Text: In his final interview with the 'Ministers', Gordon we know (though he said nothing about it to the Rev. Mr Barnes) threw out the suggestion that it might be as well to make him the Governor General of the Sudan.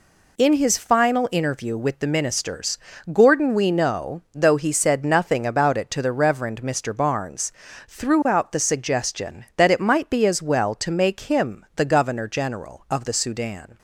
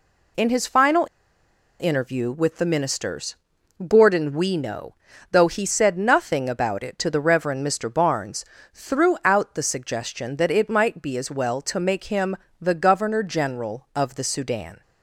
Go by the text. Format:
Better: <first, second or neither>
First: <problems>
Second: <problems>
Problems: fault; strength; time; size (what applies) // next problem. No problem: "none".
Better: first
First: none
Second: pauses between "final" and "interview"; noticeable; at 1.0 s; 0.73 s long // pauses between "him" and "the"; slight; at 12.3 s; 0.24 s long